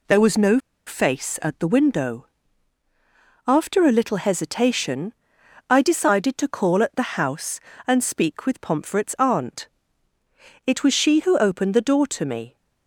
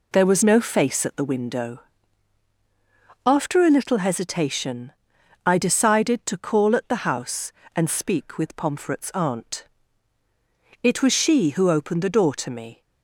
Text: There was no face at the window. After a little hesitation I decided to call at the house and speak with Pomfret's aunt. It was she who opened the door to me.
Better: second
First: pauses between "no" and "face"; slight; at 0.5 s; 0.27 s long // pauses between "hesitation" and "I"; noticeable; at 5.1 s; 0.58 s long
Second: pauses between "hesitation" and "I"; noticeable; at 4.9 s; 0.54 s long

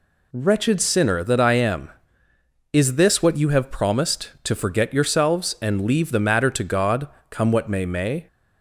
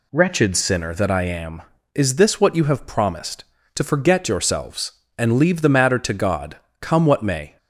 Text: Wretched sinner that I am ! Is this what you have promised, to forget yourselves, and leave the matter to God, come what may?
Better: second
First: says "may" twice; at 7.8 s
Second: none

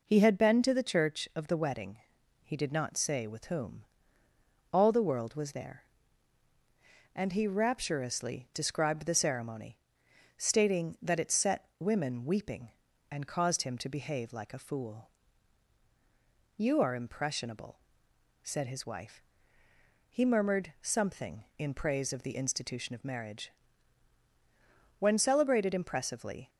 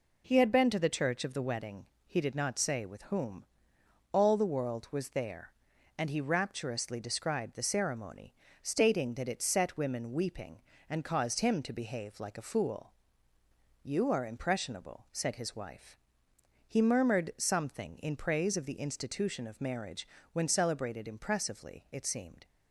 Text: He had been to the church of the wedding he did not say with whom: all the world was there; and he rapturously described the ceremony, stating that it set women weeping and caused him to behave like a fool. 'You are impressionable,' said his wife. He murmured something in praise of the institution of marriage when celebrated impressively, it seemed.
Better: second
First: pauses between "wedding" and "he"; noticeable; at 1.9 s; 0.48 s long // pauses between "marriage" and "when"; strong; at 23.5 s; 1.4 s long // stops before "it seemed"; at 26.4 s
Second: pauses between "wedding" and "he"; slight; at 1.8 s; 0.22 s long // pauses between "marriage" and "when"; slight; at 20.0 s; 0.24 s long

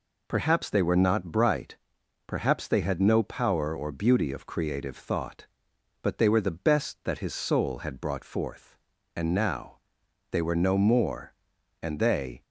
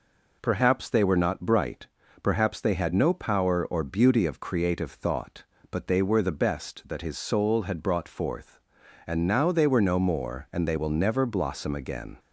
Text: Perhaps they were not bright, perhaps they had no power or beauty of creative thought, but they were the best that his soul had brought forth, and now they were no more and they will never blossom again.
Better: second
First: pauses between "now" and "they"; noticeable; at 9.7 s; 0.52 s long // stops before "will never blossom again"; at 12.4 s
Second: none

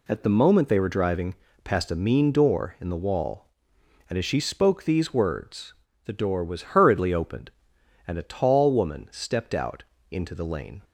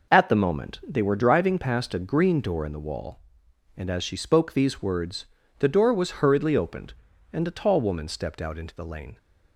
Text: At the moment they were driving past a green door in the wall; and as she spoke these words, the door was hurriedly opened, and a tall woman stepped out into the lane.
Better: second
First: pauses between "driving" and "past"; slight; at 1.3 s; 0.30 s long // says "mean" for "green"; at 1.9 s // pauses between "out" and "into"; slight; at 9.8 s; 0.30 s long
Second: none

